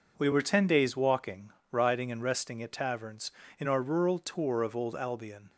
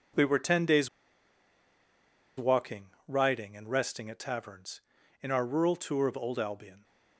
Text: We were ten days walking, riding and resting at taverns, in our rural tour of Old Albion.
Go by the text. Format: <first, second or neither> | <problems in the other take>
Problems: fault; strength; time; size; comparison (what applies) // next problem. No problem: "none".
first | pauses between "days" and "walking"; strong; at 0.8 s; 1.4 s long